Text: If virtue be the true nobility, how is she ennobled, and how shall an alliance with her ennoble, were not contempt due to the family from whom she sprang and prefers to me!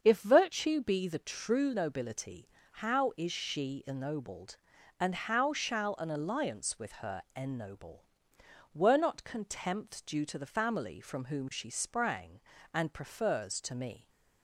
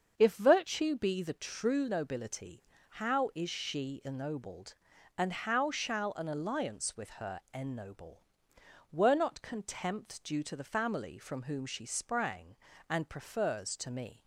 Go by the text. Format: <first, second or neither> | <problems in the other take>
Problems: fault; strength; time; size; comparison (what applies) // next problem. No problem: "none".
neither | starts louder than the rest; the same in both // pauses between "her" and "ennoble"; slight; the same in both